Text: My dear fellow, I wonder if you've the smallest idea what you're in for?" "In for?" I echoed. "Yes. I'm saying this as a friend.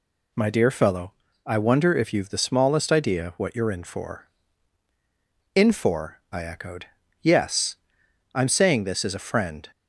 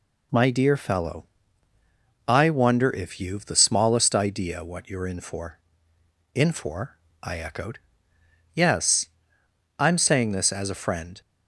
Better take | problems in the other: neither | none

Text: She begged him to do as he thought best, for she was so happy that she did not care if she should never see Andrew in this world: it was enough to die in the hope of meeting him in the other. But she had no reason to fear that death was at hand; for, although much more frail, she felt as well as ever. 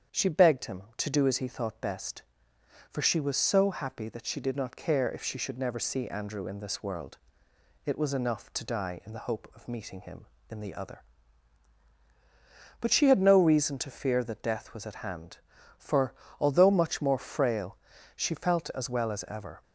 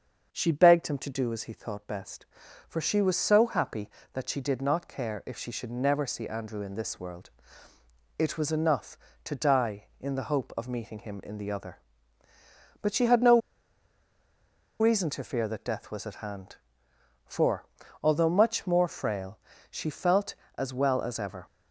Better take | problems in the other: first | starts louder than the rest; until 1.3 s; 7 dB; strong in the first // pauses between "no" and "reason"; strong; at 13.4 s; 1.3 s long

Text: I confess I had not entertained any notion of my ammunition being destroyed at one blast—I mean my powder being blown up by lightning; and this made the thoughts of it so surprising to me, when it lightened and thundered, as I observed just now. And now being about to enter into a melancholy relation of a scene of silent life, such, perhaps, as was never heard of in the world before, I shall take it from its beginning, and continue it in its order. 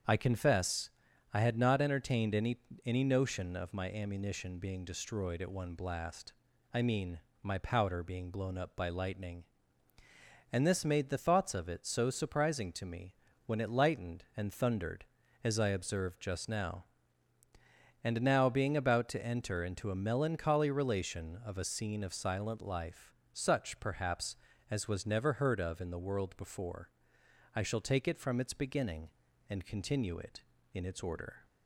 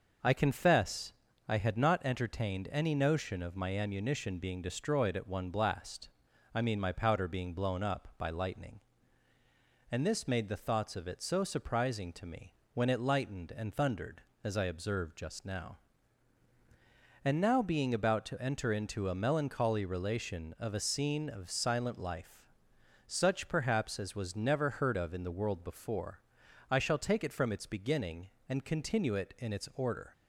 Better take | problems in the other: second | starts louder than the rest; strong; until 1.5 s; 7.5 dB; noticeable in the second // pauses between "confess" and "I"; at 0.8 s; 0.44 s long; slight in the second // says "any" twice; at 2.8 s // pauses between "mean" and "my"; slight; at 7.1 s; 0.24 s long

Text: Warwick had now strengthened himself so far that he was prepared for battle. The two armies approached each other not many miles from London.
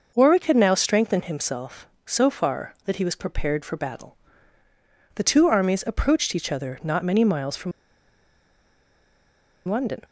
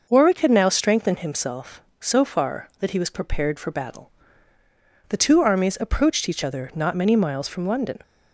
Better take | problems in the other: second | pauses between "from" and "London"; strong; at 7.7 s; 1.9 s long

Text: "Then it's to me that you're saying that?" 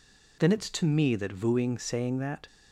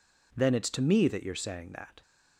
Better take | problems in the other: second | says "vooing" for "you're"; at 1.3 s

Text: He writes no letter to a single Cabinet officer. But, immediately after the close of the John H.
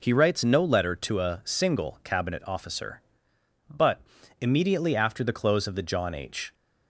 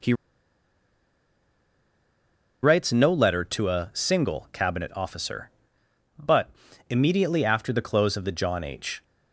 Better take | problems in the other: first | pauses between "He" and "writes"; strong; at 0.1 s; 2.4 s long

